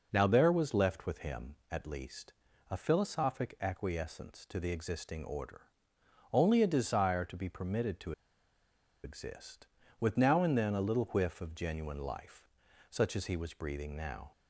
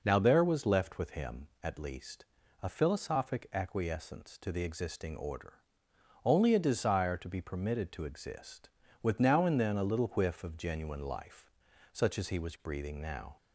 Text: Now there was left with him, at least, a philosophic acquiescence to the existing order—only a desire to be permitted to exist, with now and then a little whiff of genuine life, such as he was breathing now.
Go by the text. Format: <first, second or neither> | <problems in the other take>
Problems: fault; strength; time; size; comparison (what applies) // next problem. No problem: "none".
second | pauses between "to" and "exist"; noticeable; at 8.1 s; 0.92 s long